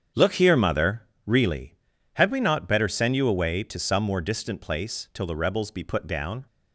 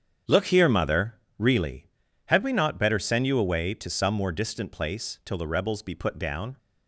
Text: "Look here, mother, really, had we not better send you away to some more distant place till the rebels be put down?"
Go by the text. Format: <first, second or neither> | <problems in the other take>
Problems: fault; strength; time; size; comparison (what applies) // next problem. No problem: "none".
neither | starts louder than the rest; strong; the same in both